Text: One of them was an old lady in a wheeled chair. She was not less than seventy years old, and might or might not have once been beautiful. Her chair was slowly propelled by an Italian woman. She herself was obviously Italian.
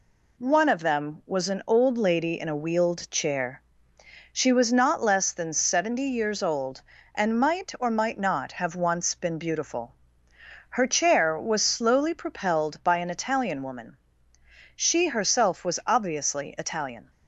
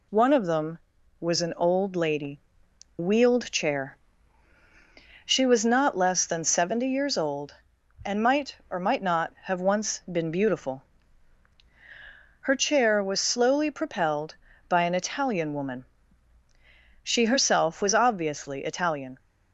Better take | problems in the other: first | skips "in a"; at 2.6 s

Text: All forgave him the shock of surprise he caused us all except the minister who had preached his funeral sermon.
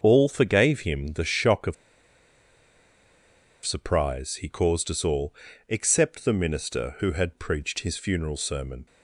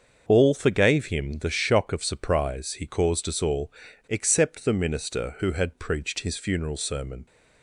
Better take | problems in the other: second | starts louder than the rest; until 1.0 s; 6.5 dB; also in the second // pauses between "of" and "surprise"; strong; at 1.7 s; 1.9 s long // pauses between "all" and "except"; slight; at 5.3 s; 0.34 s long; also in the second

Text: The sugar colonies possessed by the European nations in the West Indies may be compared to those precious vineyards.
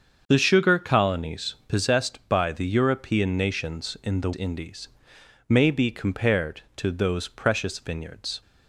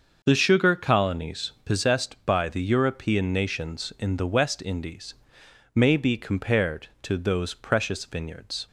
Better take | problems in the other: second | starts louder than the rest; until 1.2 s; 7 dB; also in the second // skips "West"; at 4.3 s // pauses between "Indies" and "may"; noticeable; at 4.8 s; 0.58 s long; noticeable in the second

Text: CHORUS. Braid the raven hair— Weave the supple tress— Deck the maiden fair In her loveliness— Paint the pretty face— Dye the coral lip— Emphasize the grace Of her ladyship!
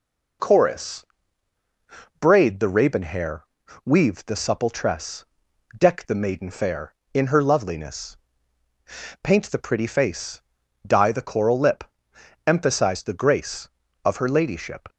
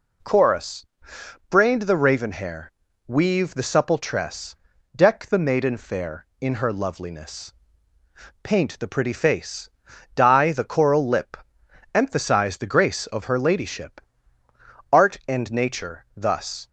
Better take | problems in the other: first | goes on to say "Art and nature thus"; strong; from 14.9 s on; 1.7 s long

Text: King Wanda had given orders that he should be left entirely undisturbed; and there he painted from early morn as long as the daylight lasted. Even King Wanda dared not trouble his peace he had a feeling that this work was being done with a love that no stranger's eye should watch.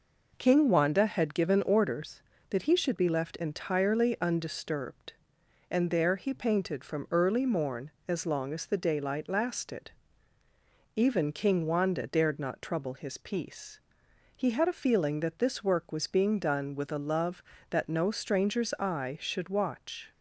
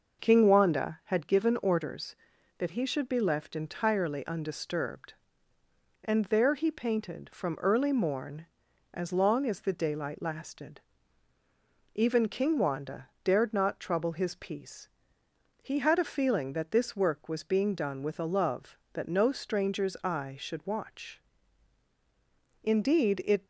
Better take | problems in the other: first | pauses between "Wanda" and "dared"; slight; at 13.0 s; 0.16 s long // pauses between "peace" and "he"; noticeable; at 14.8 s; 0.72 s long; noticeable in the first // goes on to say "Indeed it"; noticeable; from 22.6 s on; 0.82 s long

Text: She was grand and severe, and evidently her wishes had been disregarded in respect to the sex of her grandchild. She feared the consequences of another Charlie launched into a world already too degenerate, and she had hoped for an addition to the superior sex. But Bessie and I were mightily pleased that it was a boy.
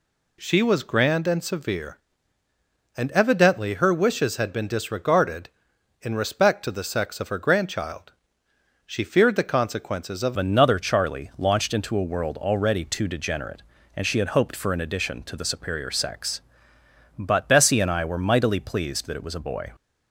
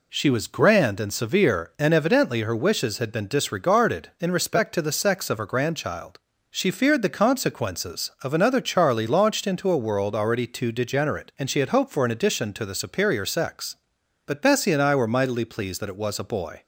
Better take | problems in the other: second | changes voice at "another"; from 10.3 s on; 9.4 s long

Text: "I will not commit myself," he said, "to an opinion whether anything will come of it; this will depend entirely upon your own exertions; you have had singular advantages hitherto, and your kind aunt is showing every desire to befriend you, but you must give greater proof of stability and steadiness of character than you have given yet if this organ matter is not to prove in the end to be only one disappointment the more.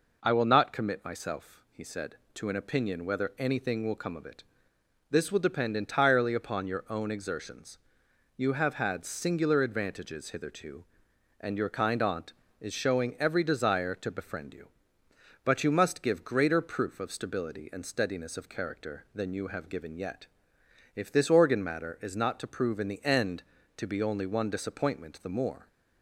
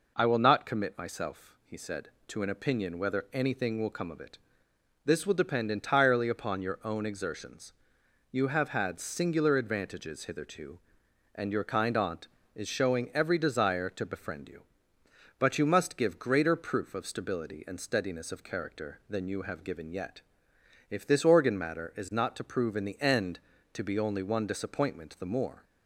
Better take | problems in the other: neither | pauses between "yet" and "if"; noticeable; the same in both

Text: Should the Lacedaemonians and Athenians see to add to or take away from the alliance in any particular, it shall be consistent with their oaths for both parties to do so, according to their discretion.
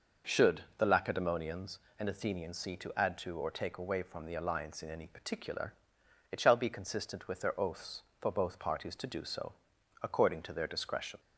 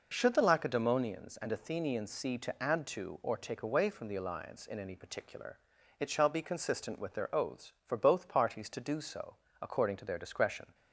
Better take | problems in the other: neither | none

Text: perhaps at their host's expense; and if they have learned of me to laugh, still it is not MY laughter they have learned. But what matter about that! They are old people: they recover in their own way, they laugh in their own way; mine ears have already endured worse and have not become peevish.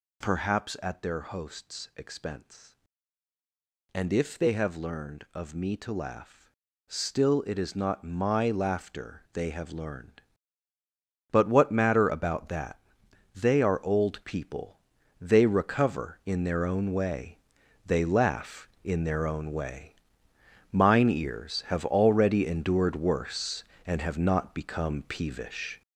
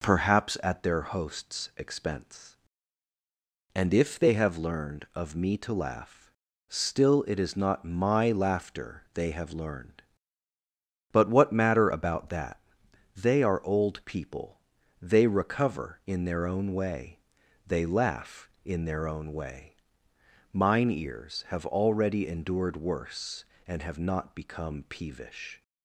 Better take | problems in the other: second | gets louder; strong; throughout; 7.5 dB

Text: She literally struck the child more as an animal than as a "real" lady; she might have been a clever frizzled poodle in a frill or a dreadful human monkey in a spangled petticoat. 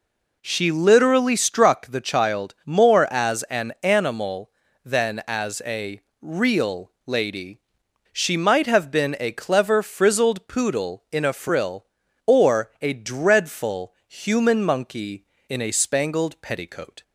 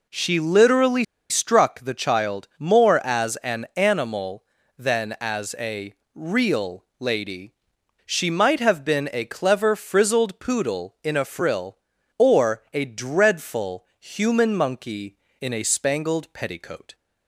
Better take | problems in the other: first | pauses between "literally" and "struck"; slight; at 1.0 s; 0.26 s long // pauses between "a" and "real"; slight; at 5.9 s; 0.22 s long; slight in the first // pauses between "dreadful" and "human"; slight; at 13.8 s; 0.16 s long; slight in the first

